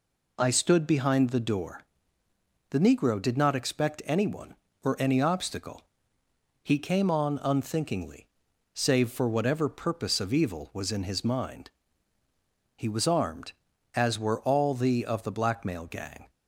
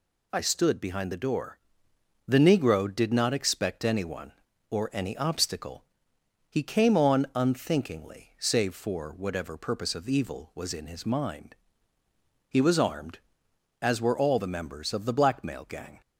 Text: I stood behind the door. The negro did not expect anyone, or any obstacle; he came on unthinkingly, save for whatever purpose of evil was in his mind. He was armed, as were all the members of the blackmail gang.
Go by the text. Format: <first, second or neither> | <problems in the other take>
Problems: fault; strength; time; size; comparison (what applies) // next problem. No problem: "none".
second | skips "members"; at 15.0 s